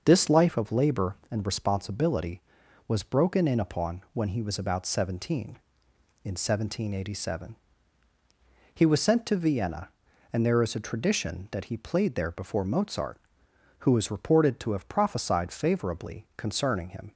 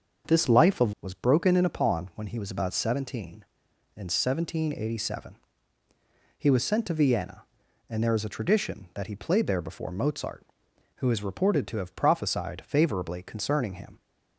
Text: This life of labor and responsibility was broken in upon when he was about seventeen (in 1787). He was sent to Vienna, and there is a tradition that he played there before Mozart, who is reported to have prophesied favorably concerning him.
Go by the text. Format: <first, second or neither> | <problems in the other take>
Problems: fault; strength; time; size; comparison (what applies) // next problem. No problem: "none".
first | starts louder than the rest; until 1.3 s; 6.5 dB; also in the first // skips "labor and responsibility"; at 0.9 s